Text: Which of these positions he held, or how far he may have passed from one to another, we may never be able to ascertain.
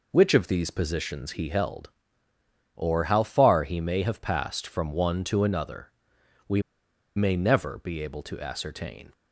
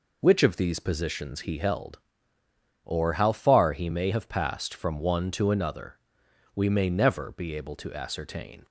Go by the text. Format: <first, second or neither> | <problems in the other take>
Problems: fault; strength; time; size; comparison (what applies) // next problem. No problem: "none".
second | pauses between "we" and "may"; noticeable; at 6.5 s; 0.56 s long